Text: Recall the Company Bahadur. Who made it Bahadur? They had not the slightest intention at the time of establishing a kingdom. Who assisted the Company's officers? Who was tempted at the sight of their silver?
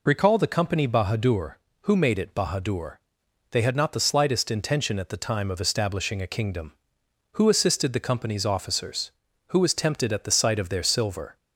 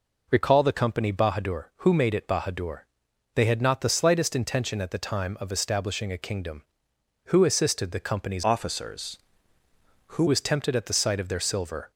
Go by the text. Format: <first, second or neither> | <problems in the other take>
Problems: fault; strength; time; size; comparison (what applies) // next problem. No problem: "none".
first | changes voice from "officers" to "Who"; from 8.4 to 10.2 s; 1.8 s long